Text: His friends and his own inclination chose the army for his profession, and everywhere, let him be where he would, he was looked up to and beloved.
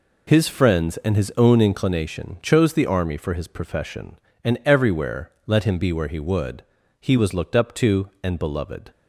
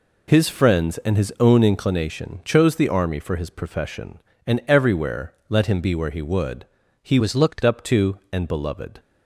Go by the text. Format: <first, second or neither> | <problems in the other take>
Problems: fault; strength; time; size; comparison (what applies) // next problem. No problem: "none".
first | changes voice from "was" to "looked"; from 7.1 to 7.6 s; 0.5 s long